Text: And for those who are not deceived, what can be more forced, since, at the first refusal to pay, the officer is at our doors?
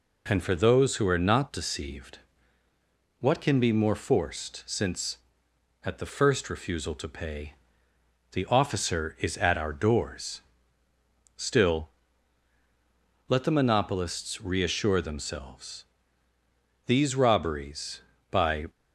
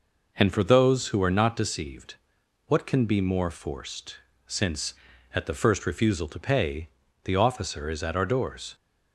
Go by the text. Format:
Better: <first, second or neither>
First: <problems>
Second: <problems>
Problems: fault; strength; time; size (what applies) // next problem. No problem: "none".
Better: second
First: goes on to say "Still let the monopolists reassure themselves These robberies by"; strong; from 11.3 s on; 7.3 s long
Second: none